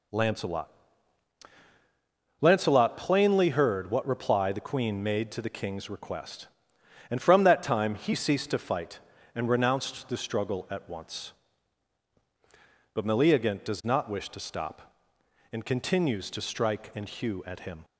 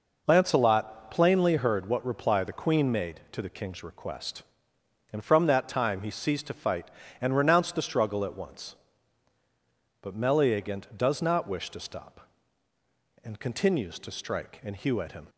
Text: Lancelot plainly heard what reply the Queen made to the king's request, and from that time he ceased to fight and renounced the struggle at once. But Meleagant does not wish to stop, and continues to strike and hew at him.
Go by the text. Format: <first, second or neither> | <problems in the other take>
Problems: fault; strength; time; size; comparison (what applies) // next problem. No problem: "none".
second | says "Lancelot" twice; at 2.3 s